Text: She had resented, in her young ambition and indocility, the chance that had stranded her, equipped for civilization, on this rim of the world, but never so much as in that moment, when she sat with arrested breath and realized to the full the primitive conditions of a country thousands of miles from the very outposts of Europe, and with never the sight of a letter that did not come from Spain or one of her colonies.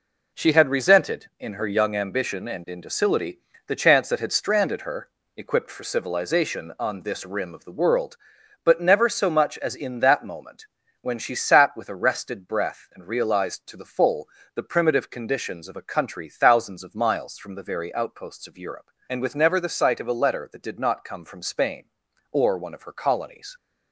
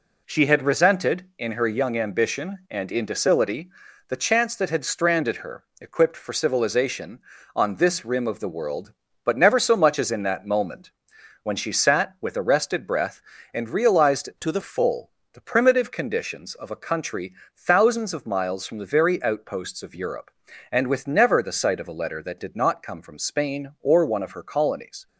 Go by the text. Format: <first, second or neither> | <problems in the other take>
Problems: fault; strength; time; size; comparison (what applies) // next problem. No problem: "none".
first | changes voice from "to" to "the"; from 14.4 to 14.6 s; 0.2 s long // pauses between "full" and "the"; slight; at 15.1 s; 0.22 s long; slight in the first // pauses between "country" and "thousands"; slight; at 17.3 s; 0.22 s long